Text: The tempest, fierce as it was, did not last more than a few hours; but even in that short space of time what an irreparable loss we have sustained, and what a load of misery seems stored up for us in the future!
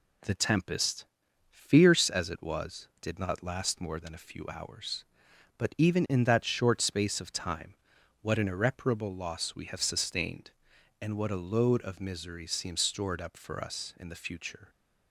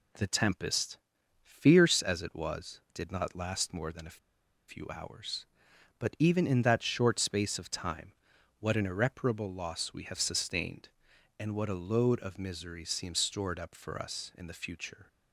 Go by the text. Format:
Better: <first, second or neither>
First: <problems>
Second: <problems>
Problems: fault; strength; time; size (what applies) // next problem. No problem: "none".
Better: first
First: pauses between "time" and "what"; noticeable; at 7.7 s; 0.48 s long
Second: pauses between "a" and "few"; noticeable; at 4.1 s; 0.50 s long // pauses between "time" and "what"; noticeable; at 8.1 s; 0.48 s long